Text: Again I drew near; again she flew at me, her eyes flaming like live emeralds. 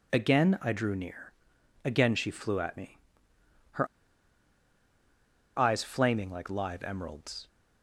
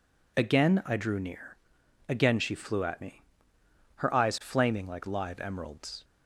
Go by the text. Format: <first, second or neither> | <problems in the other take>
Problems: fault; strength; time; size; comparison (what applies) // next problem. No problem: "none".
second | pauses between "her" and "eyes"; strong; at 3.8 s; 1.7 s long